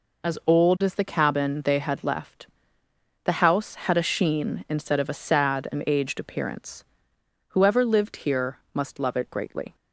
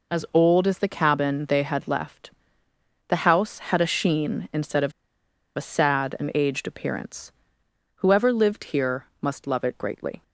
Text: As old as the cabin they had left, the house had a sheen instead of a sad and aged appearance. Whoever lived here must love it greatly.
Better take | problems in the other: first | pauses between "of" and "a"; noticeable; at 4.9 s; 0.64 s long

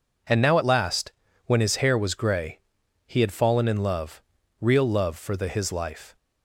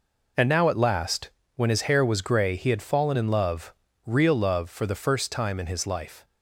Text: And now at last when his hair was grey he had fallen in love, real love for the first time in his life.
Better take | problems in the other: second | pauses between "last" and "when"; slight; at 1.1 s; 0.34 s long; slight in the second // pauses between "grey" and "he"; noticeable; at 2.5 s; 0.46 s long // skips "first time in"; at 5.4 s

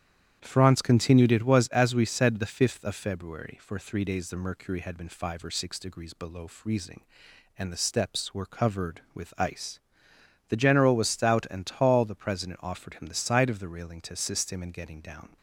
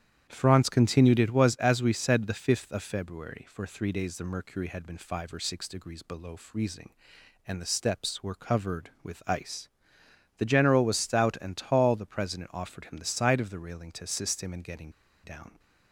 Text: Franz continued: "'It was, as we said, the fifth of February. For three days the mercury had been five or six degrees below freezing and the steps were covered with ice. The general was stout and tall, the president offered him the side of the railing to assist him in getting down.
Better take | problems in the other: first | starts louder than the rest; strong; until 1.3 s; 10 dB; strong in the first // pauses between "getting" and "down"; slight; at 14.8 s; 0.34 s long

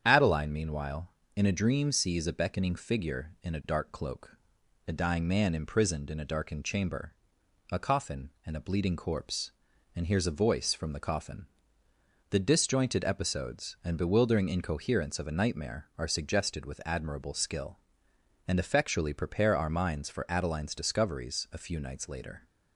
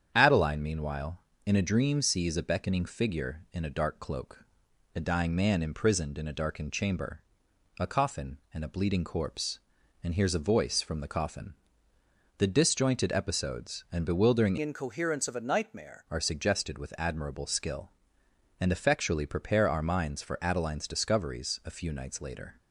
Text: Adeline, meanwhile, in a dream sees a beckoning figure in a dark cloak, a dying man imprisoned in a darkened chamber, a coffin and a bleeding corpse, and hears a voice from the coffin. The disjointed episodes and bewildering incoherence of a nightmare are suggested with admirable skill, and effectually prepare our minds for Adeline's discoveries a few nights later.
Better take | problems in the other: first | starts louder than the rest; strong; until 1.1 s; 8.5 dB; strong in the first // changes voice from "incoherence" to "nightmare"; from 14.6 to 16.0 s; 1.4 s long

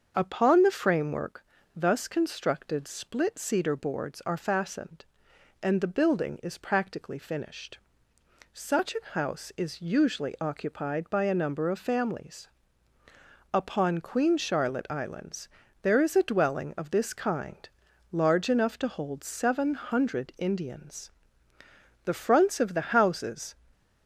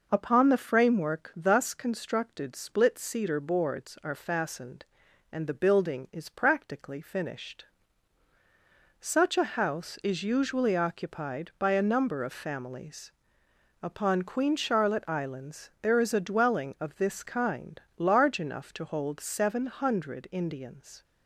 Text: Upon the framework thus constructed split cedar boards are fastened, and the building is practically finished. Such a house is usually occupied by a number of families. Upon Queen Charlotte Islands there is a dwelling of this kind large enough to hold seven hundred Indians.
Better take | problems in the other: second | starts louder than the rest; until 1.1 s; 7 dB // pauses between "framework" and "thus"; slight; at 1.4 s; 0.32 s long // pauses between "Islands" and "there"; slight; at 15.4 s; 0.32 s long // pauses between "kind" and "large"; at 17.6 s; 0.42 s long; slight in the second // goes on to say "The fronts of the houses"; from 22.0 s on; 1.5 s long

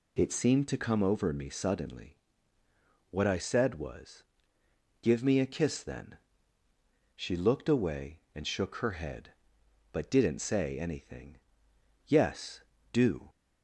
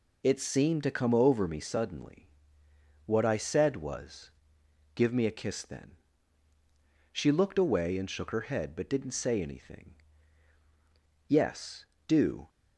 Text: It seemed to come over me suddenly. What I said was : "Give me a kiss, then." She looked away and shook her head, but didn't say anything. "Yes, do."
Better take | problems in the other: neither | none

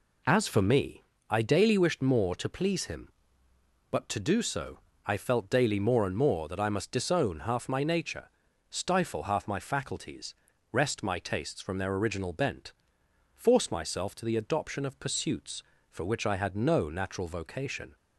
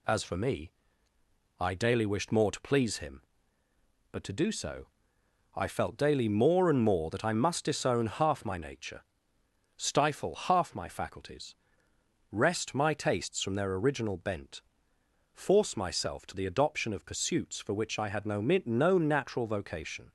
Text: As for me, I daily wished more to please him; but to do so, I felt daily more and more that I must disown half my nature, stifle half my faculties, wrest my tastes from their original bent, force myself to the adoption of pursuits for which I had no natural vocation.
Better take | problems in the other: first | says "no" twice; at 18.3 s

